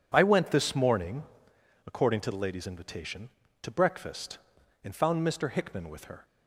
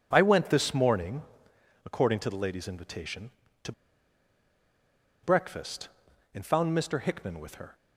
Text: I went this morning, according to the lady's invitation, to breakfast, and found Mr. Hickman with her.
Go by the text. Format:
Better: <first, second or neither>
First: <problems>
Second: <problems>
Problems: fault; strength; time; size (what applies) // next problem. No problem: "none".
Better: first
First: none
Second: pauses between "to" and "breakfast"; strong; at 3.7 s; 1.5 s long